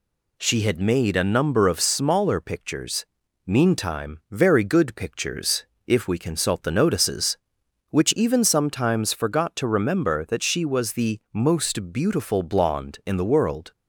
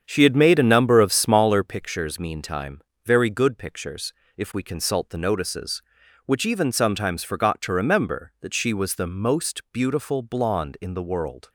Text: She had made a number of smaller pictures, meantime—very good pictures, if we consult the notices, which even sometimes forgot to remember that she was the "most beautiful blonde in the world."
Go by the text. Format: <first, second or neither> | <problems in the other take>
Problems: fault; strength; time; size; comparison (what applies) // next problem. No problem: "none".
first | starts louder than the rest; strong; until 1.7 s; 8 dB